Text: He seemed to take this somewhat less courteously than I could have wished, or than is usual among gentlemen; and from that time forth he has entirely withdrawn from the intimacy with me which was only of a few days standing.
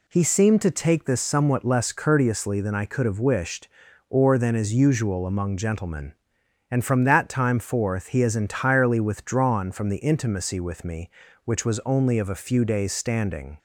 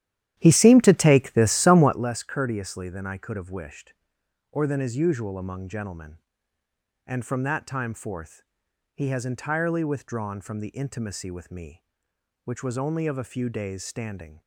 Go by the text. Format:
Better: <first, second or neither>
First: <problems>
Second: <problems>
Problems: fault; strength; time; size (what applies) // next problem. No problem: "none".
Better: first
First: none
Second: starts louder than the rest; strong; until 2.1 s; 12 dB // pauses between "forth" and "he"; noticeable; at 8.4 s; 0.50 s long